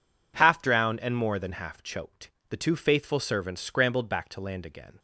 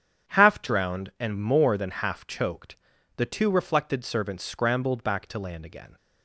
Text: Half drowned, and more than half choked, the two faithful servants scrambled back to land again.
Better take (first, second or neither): first